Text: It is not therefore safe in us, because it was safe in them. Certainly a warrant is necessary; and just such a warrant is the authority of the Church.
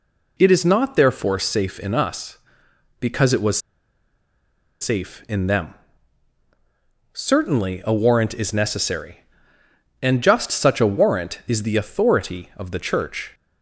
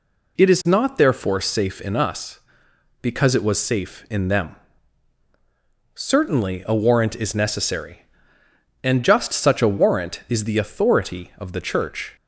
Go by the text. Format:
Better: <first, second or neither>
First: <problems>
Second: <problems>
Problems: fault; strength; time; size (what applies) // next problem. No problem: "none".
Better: second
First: pauses between "was" and "safe"; at 3.5 s; 1.2 s long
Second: none